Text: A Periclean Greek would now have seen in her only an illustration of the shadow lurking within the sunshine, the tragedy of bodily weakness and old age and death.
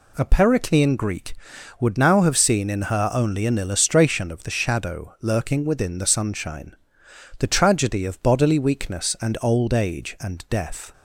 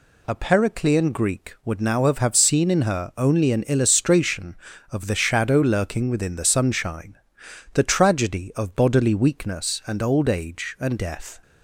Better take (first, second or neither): first